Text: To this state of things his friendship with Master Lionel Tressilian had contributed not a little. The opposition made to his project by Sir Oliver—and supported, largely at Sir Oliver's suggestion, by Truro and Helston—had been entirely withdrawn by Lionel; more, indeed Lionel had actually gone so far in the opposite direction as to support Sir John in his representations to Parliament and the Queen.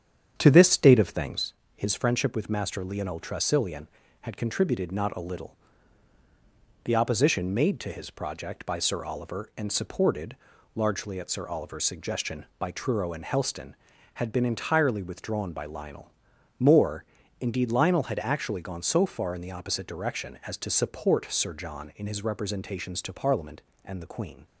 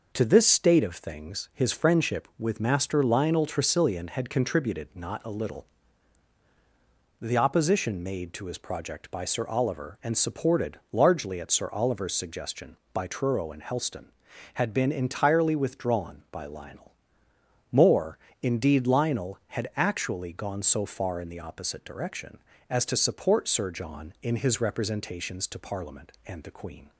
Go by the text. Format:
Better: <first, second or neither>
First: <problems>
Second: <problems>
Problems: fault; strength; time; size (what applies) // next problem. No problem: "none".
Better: second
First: starts louder than the rest; strong; until 1.6 s; 8.5 dB // pauses between "things" and "his"; slight; at 1.5 s; 0.20 s long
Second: none